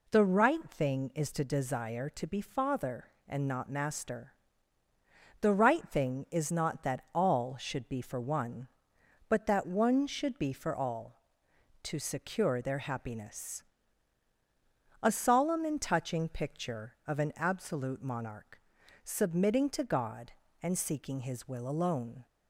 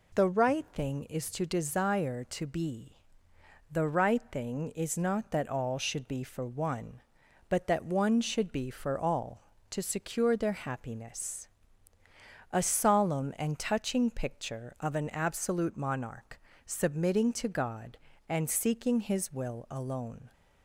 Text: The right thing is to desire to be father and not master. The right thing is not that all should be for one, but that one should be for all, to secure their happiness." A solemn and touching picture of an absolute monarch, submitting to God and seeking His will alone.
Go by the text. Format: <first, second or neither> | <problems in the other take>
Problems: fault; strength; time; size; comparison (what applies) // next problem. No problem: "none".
first | skips "father and not master"; at 3.3 s